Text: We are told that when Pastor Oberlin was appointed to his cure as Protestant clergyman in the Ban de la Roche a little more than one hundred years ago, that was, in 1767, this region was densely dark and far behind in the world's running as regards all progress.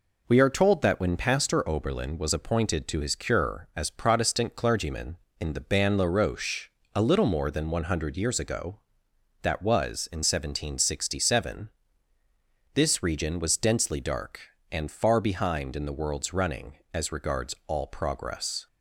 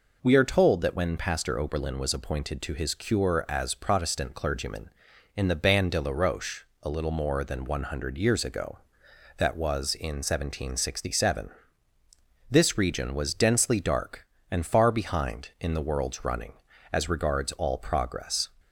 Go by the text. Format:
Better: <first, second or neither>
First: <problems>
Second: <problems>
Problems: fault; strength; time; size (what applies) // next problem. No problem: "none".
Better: second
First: skips "de"; at 5.9 s // pauses between "Roche" and "a"; slight; at 6.7 s; 0.24 s long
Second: pauses between "Roche" and "a"; slight; at 6.6 s; 0.16 s long